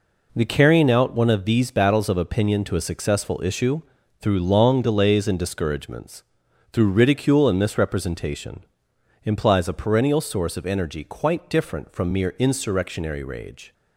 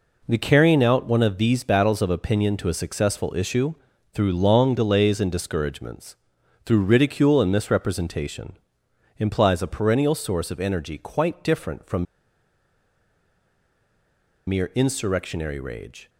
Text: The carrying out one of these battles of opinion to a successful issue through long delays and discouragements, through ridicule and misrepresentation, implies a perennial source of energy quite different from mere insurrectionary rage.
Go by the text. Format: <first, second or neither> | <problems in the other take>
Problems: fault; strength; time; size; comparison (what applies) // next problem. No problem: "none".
first | pauses between "issue" and "through"; at 3.7 s; 0.40 s long; also in the first // pauses between "from" and "mere"; strong; at 12.0 s; 2.4 s long